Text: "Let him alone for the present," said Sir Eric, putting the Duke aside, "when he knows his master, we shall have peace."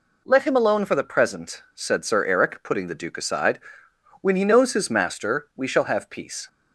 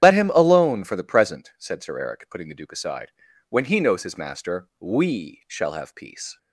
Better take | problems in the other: first | loses the start of "Let"; at 0.0 s; 55 ms // starts louder than the rest; strong; until 1.0 s; 10 dB

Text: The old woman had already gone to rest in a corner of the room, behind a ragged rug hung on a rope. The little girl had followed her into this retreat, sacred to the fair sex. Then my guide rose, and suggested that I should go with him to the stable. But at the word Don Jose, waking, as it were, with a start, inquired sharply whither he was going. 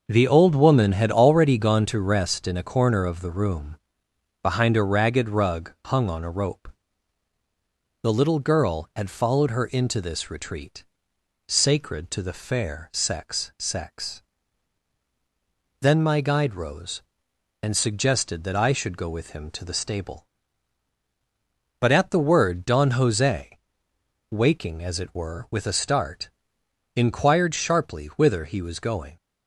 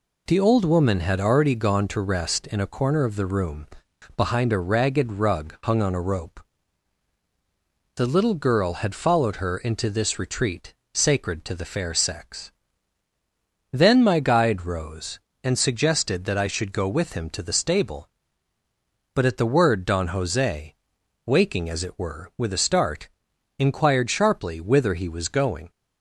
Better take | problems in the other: second | says "sex" twice; at 13.5 s

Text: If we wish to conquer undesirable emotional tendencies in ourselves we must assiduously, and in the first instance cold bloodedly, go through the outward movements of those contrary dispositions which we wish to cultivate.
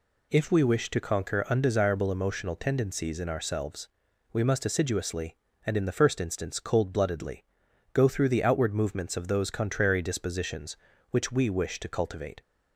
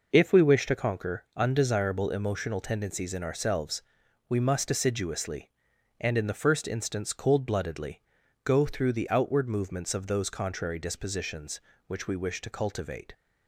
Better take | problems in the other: neither | pauses between "ourselves" and "we"; noticeable; the same in both

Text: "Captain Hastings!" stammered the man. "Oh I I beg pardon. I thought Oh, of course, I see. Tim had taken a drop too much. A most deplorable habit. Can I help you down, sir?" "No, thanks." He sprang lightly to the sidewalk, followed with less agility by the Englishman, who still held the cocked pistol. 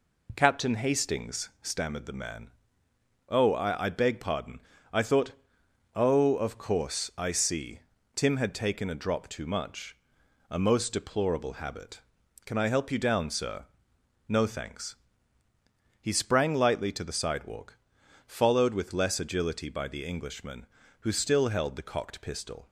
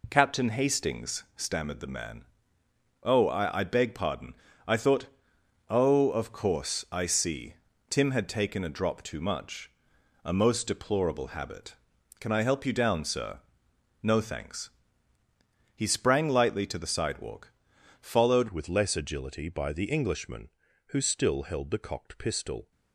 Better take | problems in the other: first | pauses between "thought" and "Oh"; noticeable; at 5.0 s; 0.60 s long; noticeable in the first // changes voice at "with"; from 18.4 s on; 4.3 s long

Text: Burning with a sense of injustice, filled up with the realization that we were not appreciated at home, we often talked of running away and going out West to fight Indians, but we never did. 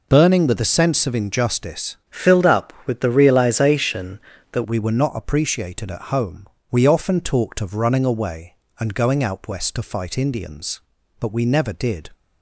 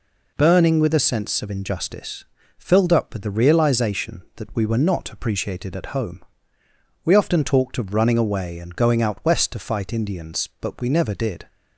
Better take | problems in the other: second | changes voice from "filled" to "that"; from 2.0 to 4.6 s; 2.6 s long

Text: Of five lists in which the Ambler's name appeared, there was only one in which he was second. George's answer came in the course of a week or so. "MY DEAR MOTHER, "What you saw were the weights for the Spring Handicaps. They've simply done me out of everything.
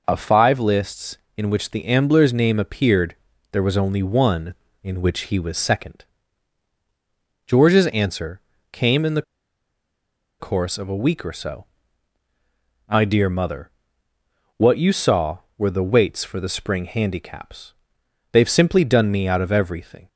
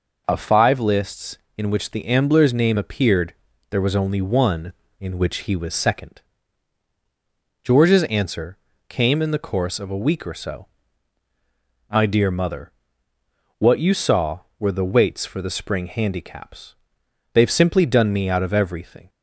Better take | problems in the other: second | pauses between "answer" and "came"; slight; at 8.4 s; 0.30 s long; slight in the second // pauses between "the" and "course"; at 9.2 s; 1.1 s long

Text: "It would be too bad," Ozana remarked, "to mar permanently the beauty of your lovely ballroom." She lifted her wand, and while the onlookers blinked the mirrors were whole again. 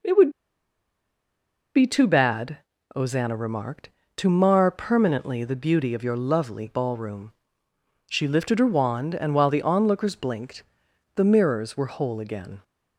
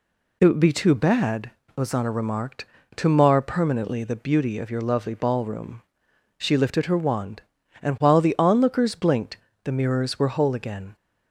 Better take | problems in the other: second | pauses between "would" and "be"; strong; at 0.3 s; 1.4 s long // pauses between "blinked" and "the"; noticeable; at 10.6 s; 0.54 s long; slight in the second

